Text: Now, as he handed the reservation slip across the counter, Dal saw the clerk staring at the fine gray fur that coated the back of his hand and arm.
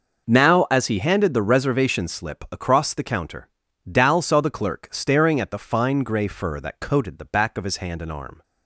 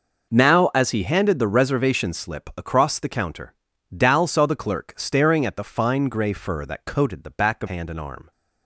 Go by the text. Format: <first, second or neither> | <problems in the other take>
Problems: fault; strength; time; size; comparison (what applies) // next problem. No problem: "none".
first | skips "his"; at 7.6 s